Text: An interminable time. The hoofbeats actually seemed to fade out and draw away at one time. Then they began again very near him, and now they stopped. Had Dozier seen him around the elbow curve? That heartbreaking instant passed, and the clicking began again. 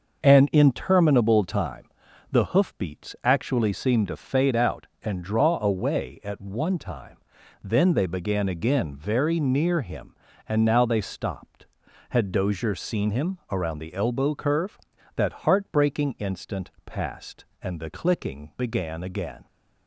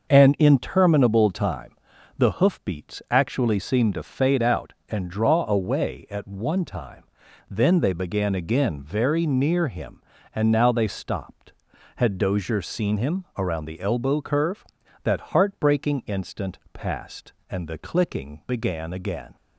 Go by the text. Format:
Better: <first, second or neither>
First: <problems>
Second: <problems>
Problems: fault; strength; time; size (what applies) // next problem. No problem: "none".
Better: neither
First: starts louder than the rest; noticeable; until 1.2 s; 6 dB // pauses between "instant" and "passed"; slight; at 16.6 s; 0.16 s long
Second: starts louder than the rest; noticeable; until 1.1 s; 6 dB // pauses between "instant" and "passed"; slight; at 16.5 s; 0.16 s long